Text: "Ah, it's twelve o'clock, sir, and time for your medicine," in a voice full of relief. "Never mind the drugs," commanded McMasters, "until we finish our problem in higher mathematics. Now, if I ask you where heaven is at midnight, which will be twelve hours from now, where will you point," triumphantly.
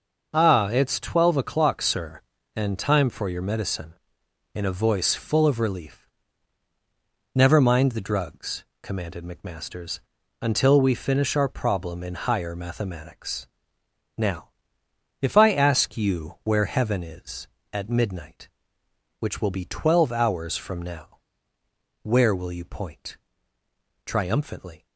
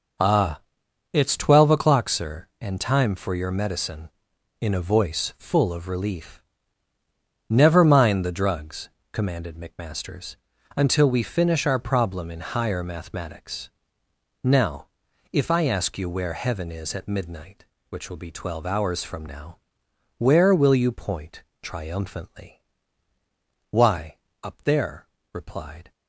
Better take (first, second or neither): first